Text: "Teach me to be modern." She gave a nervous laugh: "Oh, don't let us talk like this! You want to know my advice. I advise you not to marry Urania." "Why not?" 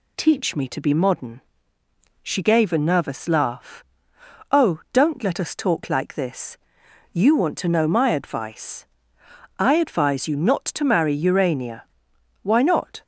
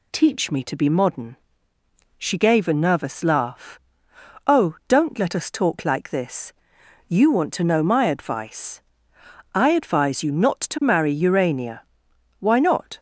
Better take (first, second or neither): neither